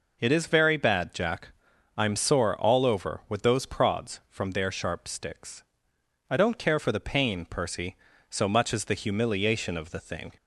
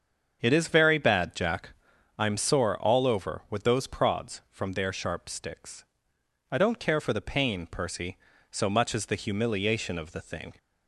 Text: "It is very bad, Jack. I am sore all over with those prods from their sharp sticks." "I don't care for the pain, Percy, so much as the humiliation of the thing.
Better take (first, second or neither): first